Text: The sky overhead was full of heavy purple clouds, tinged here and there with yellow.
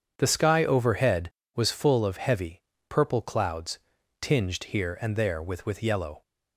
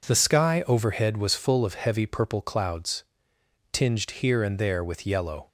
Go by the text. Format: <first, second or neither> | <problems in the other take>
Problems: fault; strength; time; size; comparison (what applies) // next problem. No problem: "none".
second | starts louder than the rest; strong; until 1.1 s; 7.5 dB // pauses between "heavy" and "purple"; slight; at 2.6 s; 0.26 s long // says "with" twice; at 5.6 s